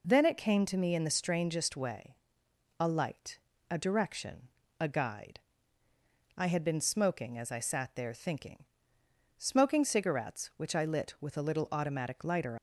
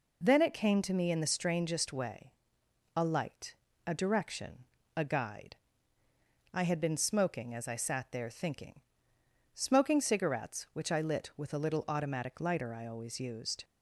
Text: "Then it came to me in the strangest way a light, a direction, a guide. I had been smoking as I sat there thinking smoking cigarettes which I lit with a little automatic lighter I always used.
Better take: second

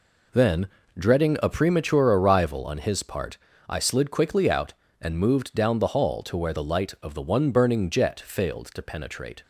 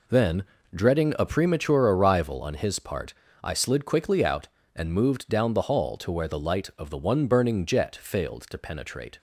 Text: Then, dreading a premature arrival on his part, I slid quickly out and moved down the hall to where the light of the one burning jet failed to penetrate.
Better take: neither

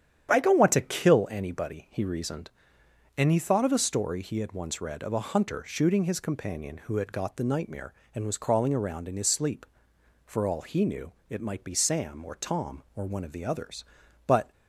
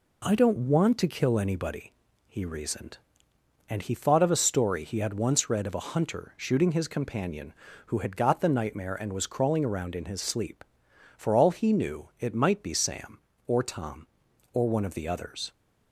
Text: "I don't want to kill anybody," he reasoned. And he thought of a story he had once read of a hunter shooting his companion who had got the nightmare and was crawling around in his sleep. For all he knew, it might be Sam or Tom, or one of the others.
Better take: second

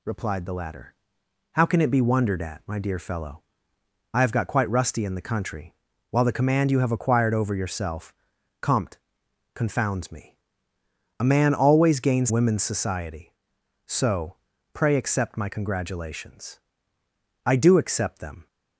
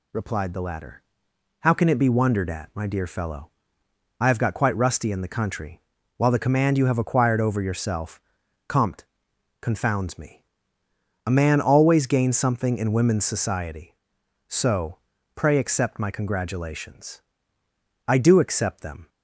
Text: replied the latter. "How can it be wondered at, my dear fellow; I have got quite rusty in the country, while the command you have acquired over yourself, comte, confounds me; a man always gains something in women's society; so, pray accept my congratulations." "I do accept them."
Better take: second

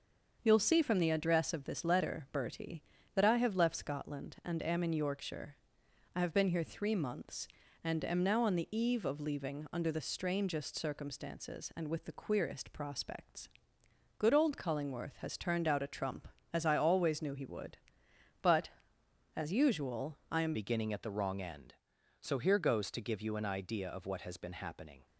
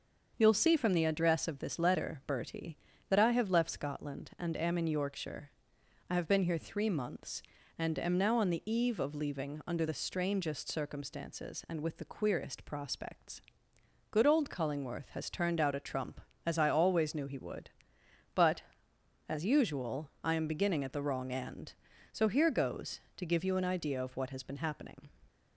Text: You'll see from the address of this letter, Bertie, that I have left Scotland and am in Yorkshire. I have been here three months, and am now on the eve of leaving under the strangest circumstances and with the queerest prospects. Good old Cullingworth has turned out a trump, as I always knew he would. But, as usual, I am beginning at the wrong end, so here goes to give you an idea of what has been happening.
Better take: second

